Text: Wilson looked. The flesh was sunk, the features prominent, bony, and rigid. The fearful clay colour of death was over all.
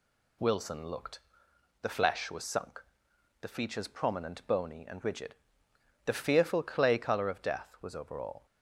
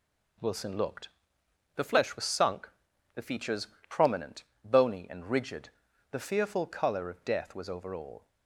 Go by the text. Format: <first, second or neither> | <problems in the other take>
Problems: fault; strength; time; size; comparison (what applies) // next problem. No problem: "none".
first | pauses between "features" and "prominent"; slight; at 3.6 s; 0.22 s long // skips "clay"; at 6.6 s